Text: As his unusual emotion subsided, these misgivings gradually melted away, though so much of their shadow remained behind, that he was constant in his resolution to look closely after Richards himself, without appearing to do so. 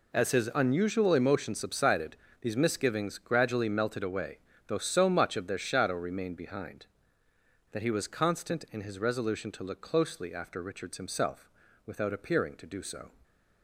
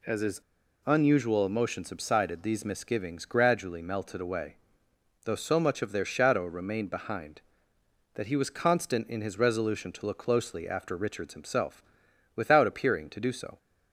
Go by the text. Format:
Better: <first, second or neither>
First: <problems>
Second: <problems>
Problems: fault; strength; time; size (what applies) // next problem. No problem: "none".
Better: first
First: none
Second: pauses between "his" and "unusual"; at 0.4 s; 0.45 s long